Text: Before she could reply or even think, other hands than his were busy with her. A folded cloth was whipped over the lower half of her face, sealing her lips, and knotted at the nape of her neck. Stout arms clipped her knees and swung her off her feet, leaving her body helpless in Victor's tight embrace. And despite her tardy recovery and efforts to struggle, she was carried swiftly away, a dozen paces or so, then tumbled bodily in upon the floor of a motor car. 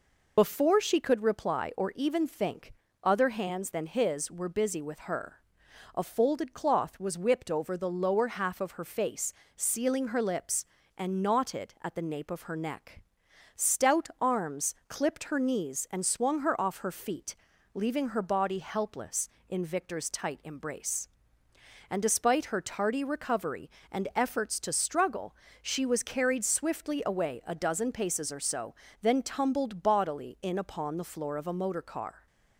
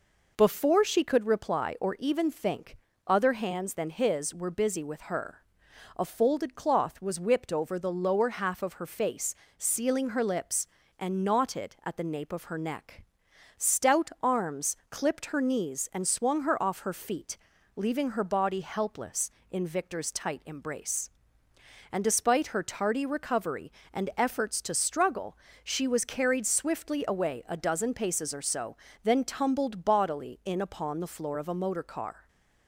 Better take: second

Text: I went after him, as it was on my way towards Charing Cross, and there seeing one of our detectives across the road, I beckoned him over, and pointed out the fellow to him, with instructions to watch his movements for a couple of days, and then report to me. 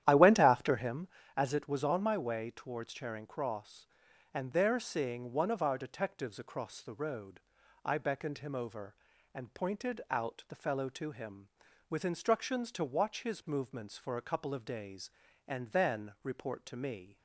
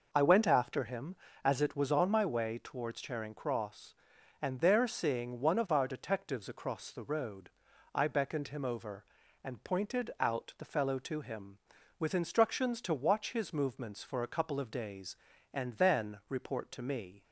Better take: second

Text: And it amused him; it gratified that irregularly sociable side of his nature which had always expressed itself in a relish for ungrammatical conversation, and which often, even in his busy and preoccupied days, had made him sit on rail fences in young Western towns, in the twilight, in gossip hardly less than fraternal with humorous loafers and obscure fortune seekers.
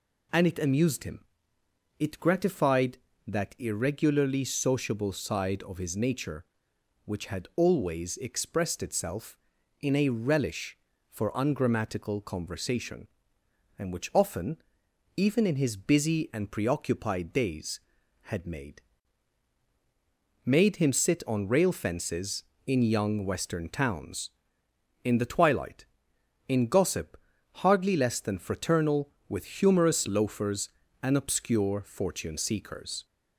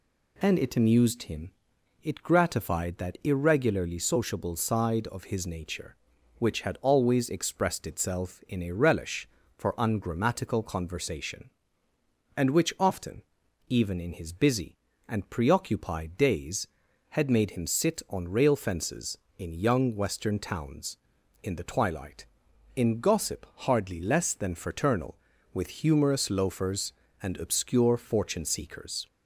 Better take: second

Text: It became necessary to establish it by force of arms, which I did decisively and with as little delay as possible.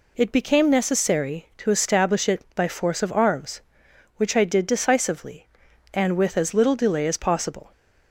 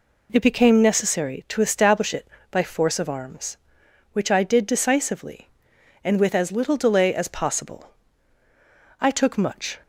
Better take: first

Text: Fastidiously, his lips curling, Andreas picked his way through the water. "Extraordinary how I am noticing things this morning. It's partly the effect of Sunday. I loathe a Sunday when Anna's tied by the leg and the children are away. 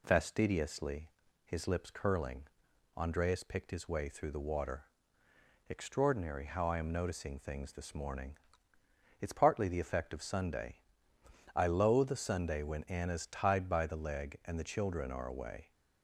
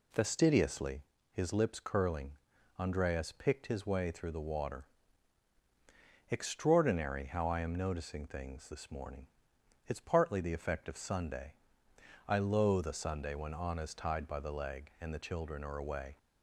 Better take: neither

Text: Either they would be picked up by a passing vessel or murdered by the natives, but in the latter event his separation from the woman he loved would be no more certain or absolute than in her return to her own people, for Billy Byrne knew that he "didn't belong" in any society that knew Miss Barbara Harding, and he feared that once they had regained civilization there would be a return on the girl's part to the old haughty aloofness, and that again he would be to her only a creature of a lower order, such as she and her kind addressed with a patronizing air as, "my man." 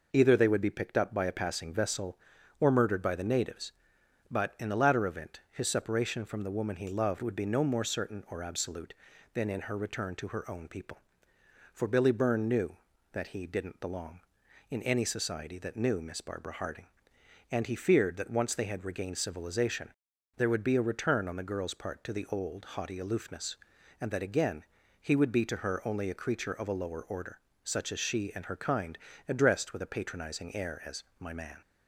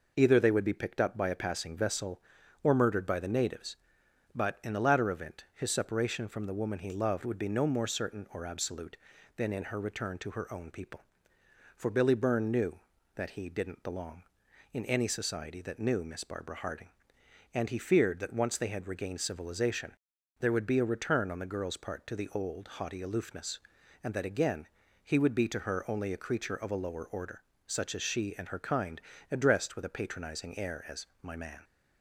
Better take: neither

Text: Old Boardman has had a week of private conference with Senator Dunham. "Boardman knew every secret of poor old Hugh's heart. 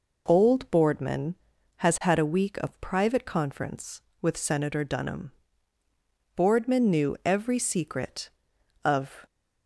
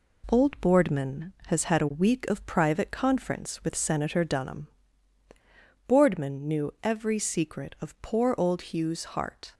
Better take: second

